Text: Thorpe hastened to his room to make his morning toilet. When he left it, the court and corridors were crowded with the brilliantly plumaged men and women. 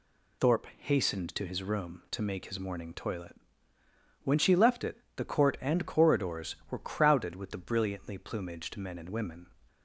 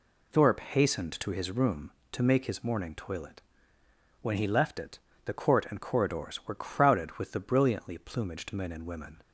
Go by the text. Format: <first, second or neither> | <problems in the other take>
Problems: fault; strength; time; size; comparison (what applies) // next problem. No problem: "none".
second | says "she" for "he"; at 4.3 s